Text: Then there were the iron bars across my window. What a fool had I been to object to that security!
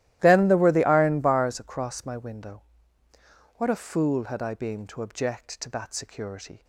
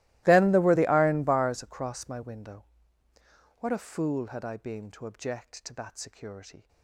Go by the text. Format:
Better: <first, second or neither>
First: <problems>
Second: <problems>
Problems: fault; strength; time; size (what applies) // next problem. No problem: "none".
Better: first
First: starts louder than the rest; strong; until 1.2 s; 14.5 dB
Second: gets quieter; strong; throughout; 25.5 dB // starts louder than the rest; strong; until 1.2 s; 18 dB